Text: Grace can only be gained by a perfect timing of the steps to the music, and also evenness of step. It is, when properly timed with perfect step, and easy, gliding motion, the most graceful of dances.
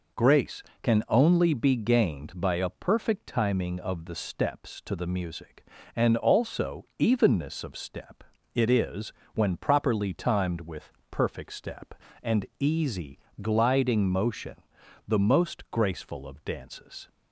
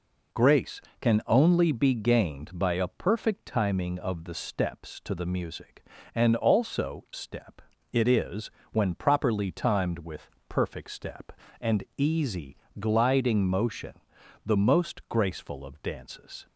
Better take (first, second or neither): first